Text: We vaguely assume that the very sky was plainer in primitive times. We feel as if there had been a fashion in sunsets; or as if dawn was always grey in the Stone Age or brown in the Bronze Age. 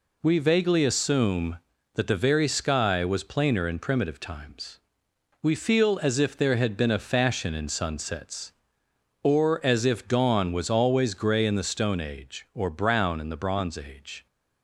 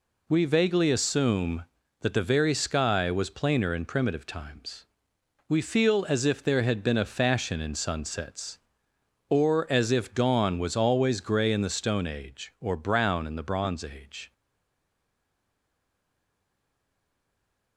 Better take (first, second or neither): first